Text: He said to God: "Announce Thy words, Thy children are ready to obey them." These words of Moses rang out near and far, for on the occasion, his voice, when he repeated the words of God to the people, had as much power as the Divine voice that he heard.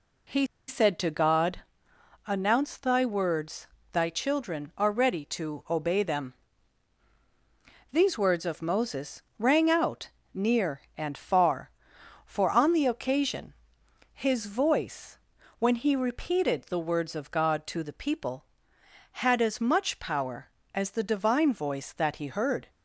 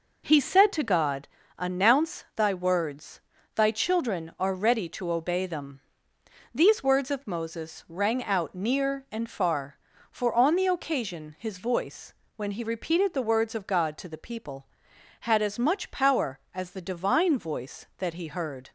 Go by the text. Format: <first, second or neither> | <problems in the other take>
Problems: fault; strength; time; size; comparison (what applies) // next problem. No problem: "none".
second | pauses between "He" and "said"; slight; at 0.4 s; 0.22 s long // pauses between "Moses" and "rang"; slight; at 9.2 s; 0.16 s long // pauses between "out" and "near"; slight; at 10.0 s; 0.24 s long